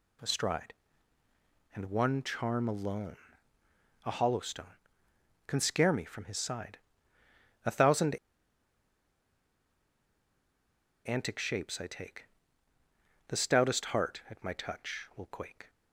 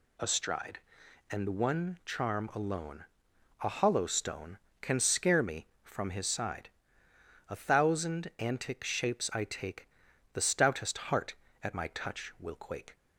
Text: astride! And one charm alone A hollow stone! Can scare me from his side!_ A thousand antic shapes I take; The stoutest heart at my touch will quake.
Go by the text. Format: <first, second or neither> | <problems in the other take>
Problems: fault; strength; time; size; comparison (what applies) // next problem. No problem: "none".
second | pauses between "alone" and "A"; noticeable; at 3.1 s; 0.88 s long; noticeable in the second // pauses between "thousand" and "antic"; strong; at 8.1 s; 2.9 s long